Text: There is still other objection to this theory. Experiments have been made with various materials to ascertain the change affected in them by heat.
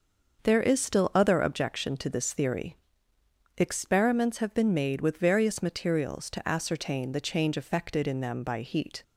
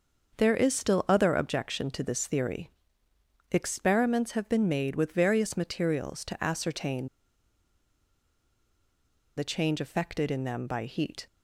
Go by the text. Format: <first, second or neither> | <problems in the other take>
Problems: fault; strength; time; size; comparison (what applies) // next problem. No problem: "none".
first | starts louder than the rest; until 1.4 s; 6.5 dB; also in the first // pauses between "ascertain" and "the"; strong; at 7.0 s; 2.3 s long